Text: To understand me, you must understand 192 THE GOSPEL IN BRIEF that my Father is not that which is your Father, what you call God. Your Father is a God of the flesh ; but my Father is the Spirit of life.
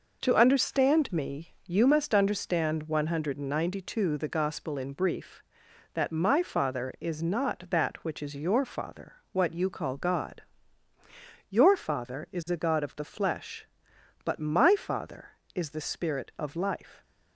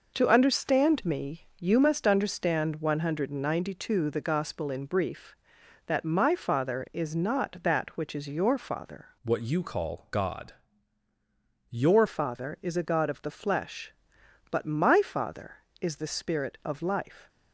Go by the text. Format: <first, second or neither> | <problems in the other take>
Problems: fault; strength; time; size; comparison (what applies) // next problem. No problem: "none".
first | changes voice from "what" to "Your"; from 9.2 to 12.0 s; 2.8 s long